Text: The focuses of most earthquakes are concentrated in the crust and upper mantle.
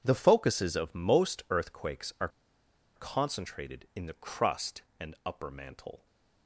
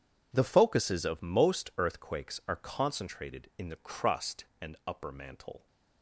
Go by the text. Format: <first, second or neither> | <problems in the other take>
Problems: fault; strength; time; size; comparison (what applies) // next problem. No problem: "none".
second | pauses between "are" and "concentrated"; noticeable; at 2.2 s; 0.67 s long